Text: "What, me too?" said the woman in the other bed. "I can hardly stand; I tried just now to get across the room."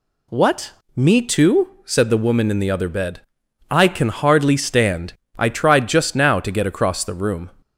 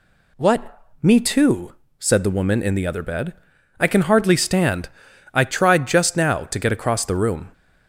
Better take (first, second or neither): neither